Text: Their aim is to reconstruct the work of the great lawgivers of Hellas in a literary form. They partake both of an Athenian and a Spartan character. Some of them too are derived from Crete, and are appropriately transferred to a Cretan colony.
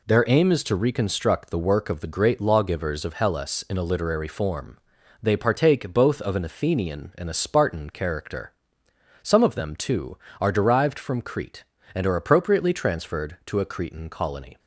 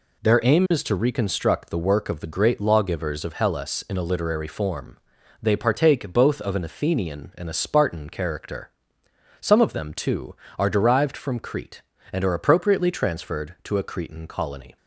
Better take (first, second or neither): neither